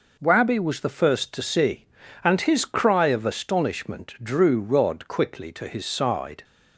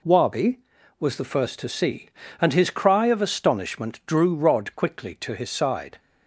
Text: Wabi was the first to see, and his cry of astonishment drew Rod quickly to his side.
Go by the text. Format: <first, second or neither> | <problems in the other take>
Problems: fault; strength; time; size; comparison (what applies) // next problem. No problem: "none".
neither | none